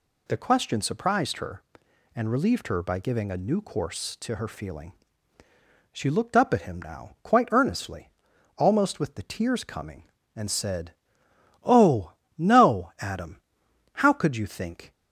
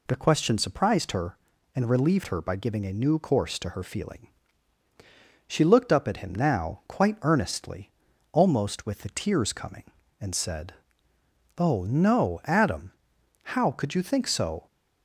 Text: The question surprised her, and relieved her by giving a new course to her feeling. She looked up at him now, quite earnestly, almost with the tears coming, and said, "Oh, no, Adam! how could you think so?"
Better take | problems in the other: second | stops before "so"; at 14.9 s

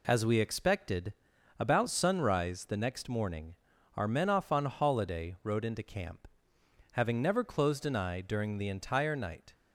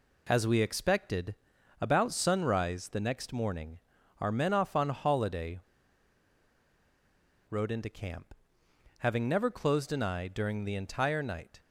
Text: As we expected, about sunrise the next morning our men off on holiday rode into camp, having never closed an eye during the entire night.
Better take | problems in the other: first | pauses between "morning" and "our"; at 3.7 s; 0.42 s long; also in the first // pauses between "holiday" and "rode"; strong; at 5.5 s; 1.9 s long

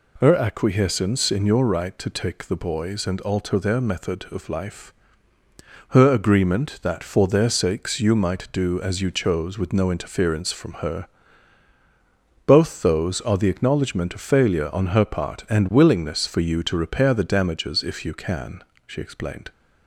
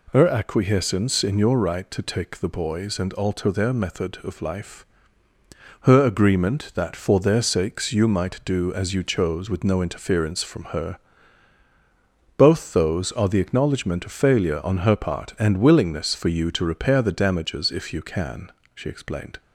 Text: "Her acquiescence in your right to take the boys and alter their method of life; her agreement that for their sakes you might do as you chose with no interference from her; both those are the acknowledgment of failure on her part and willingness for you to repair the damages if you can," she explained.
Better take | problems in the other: neither | none

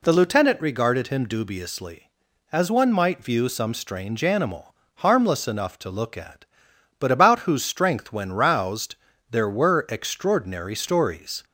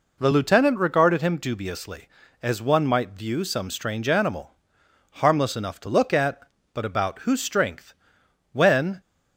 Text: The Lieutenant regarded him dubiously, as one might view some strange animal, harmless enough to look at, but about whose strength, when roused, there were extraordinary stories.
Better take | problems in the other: first | stops before "roused there were extraordinary stories"; at 8.9 s

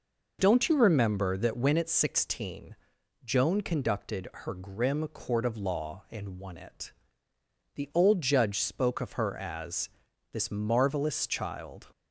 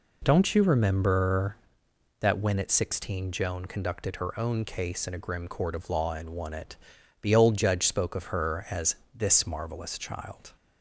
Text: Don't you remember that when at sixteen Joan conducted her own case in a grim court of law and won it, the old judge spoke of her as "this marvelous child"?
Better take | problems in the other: second | pauses between "sixteen" and "Joan"; noticeable; at 2.7 s; 0.48 s long // skips "own case in a"; at 4.5 s // pauses between "as" and "this"; at 9.8 s; 0.42 s long; slight in the second

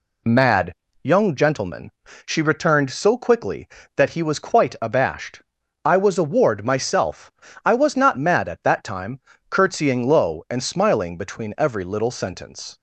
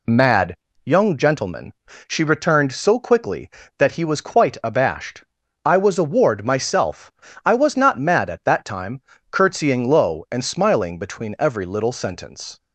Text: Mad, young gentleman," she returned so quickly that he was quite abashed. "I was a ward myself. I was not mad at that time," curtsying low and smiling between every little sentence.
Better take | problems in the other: neither | none

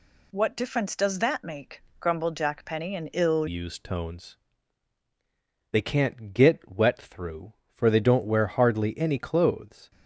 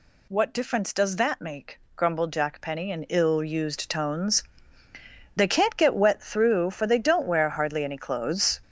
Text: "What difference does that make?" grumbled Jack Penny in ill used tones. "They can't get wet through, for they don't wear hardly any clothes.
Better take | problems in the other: second | changes voice at "used"; from 3.4 s on; 6.5 s long

